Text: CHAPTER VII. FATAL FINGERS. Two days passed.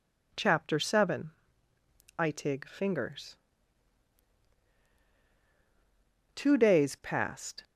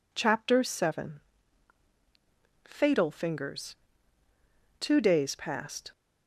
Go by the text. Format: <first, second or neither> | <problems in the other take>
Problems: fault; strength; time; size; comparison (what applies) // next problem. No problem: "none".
second | says "Itig" for "FATAL"; at 2.1 s